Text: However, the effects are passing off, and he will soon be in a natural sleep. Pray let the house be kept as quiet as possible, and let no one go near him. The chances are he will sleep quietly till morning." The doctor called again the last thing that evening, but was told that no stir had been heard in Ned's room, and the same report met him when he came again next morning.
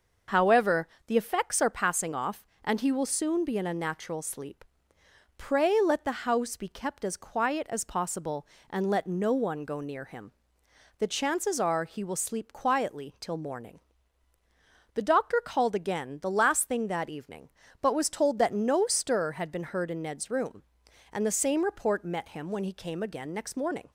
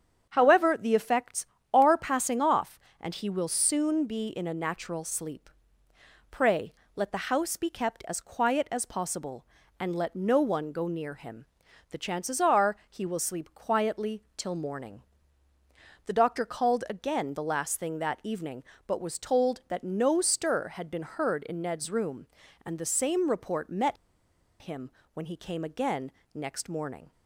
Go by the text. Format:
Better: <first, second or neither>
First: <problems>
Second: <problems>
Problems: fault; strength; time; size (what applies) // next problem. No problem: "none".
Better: first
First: starts louder than the rest; until 1.4 s; 6 dB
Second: starts louder than the rest; strong; until 1.3 s; 8 dB // pauses between "Pray" and "let"; slight; at 6.7 s; 0.22 s long // pauses between "met" and "him"; noticeable; at 23.9 s; 0.65 s long // pauses between "him" and "when"; slight; at 24.8 s; 0.24 s long // pauses between "again" and "next"; slight; at 26.1 s; 0.22 s long